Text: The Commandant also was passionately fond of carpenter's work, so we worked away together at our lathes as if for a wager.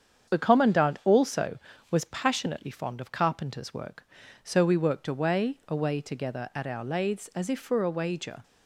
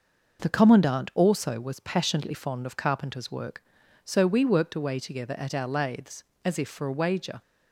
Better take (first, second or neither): second